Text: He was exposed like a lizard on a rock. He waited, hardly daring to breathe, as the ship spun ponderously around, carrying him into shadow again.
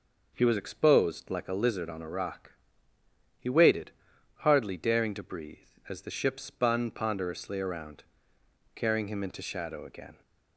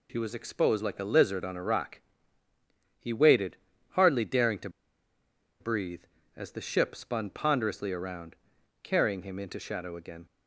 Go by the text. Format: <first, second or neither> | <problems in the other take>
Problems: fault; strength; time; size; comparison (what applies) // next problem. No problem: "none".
first | pauses between "to" and "breathe"; noticeable; at 4.6 s; 0.91 s long